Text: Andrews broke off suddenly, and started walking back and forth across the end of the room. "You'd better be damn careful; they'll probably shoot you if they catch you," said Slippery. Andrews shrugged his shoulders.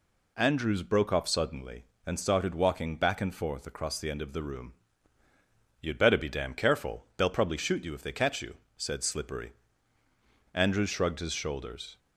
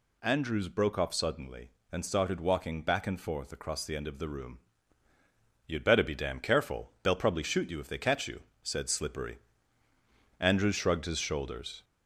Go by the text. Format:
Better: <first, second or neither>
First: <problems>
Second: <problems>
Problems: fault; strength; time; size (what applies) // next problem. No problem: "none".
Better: first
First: none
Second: gets louder; slight; throughout; 3 dB